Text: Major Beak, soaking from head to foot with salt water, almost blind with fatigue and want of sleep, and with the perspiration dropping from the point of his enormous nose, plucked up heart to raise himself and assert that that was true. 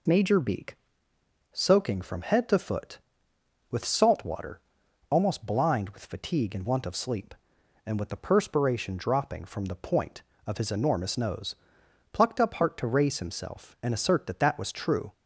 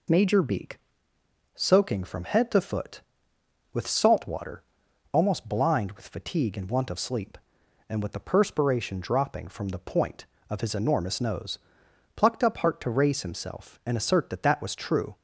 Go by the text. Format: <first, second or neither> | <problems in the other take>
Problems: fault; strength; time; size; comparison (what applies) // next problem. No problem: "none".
neither | none